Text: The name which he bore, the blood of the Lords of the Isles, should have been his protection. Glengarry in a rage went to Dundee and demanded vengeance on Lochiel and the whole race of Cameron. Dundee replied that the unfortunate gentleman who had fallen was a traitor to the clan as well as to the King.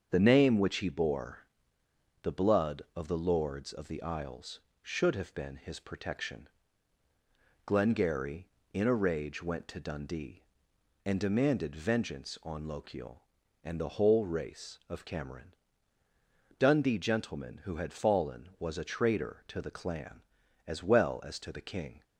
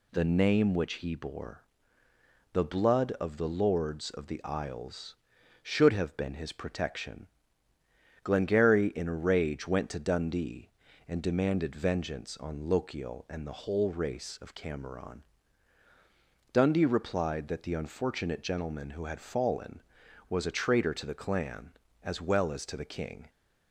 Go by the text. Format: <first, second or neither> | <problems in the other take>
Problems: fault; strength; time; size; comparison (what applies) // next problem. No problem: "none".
second | starts louder than the rest; strong; until 1.1 s; 7 dB // skips "replied that the unfortunate"; at 16.9 s